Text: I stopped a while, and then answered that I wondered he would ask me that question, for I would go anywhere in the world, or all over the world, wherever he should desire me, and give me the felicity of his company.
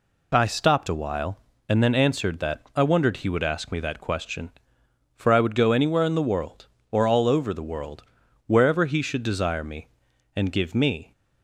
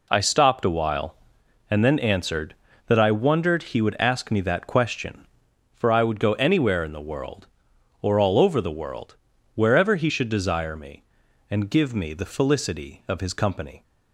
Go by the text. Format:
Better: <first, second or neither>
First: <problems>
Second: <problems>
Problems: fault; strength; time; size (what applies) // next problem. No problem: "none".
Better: second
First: stops before "the felicity of his company"; at 11.1 s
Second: none